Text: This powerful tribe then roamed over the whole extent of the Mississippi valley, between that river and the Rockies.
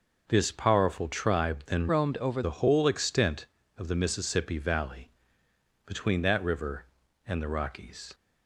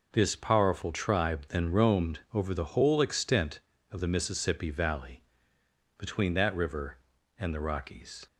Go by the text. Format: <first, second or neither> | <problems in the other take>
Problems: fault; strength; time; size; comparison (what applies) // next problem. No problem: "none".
second | changes voice from "roamed" to "over"; from 1.8 to 2.4 s; 0.6 s long